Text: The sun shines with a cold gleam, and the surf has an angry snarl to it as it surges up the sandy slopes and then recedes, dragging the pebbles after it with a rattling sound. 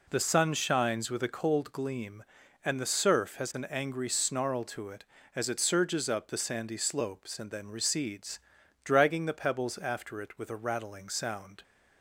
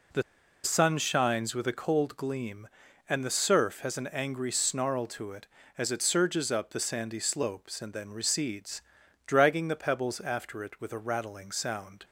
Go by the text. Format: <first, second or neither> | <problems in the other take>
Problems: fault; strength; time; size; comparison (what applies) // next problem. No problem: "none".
first | pauses between "The" and "sun"; at 0.2 s; 0.42 s long